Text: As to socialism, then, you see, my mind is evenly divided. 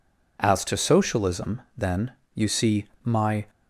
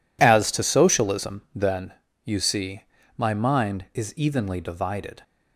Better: second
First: stops before "mind is evenly divided"; at 3.4 s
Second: none

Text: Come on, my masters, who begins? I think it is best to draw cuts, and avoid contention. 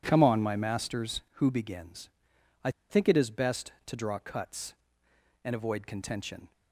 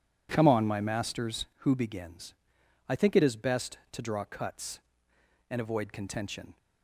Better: second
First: pauses between "I" and "think"; slight; at 2.7 s; 0.19 s long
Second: none

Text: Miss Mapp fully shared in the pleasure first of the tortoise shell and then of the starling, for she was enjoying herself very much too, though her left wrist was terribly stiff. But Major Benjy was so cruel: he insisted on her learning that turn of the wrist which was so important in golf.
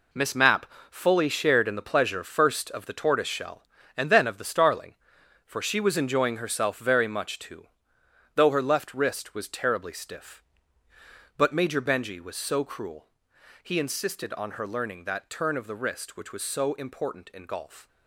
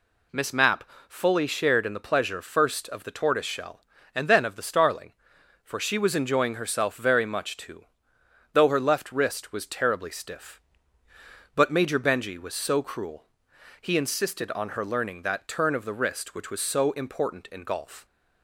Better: second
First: gets quieter; strong; throughout; 9.5 dB // pauses between "Mapp" and "fully"; slight; at 0.6 s; 0.24 s long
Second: pauses between "Mapp" and "fully"; slight; at 0.8 s; 0.24 s long

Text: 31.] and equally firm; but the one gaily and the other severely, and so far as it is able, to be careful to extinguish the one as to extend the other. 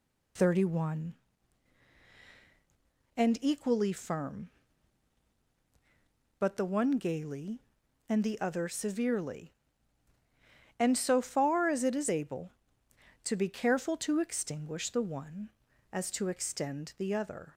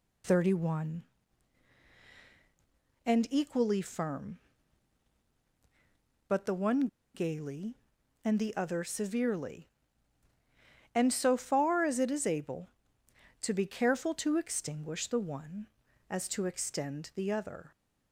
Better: first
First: none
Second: pauses between "one" and "gaily"; slight; at 6.8 s; 0.27 s long

